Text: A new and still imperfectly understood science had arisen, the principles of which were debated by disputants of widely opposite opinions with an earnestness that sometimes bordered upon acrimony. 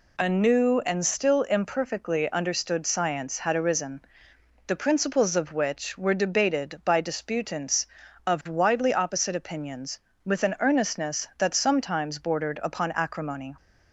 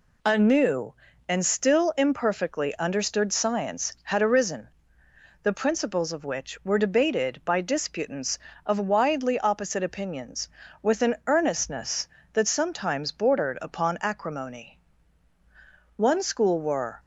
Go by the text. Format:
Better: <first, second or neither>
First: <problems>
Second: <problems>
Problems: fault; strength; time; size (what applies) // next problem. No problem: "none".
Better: first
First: none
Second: goes on to say "One school were"; noticeable; from 15.9 s on; 1.0 s long